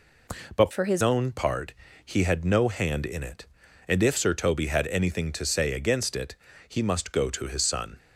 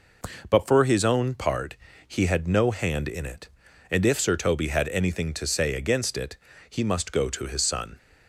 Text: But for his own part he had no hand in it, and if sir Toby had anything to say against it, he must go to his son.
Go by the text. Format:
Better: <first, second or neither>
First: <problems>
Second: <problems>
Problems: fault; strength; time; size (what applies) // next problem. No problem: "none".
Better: second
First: changes voice from "for" to "his"; from 0.7 to 1.0 s; 0.3 s long // pauses between "part" and "he"; slight; at 1.7 s; 0.30 s long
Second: pauses between "part" and "he"; slight; at 1.7 s; 0.30 s long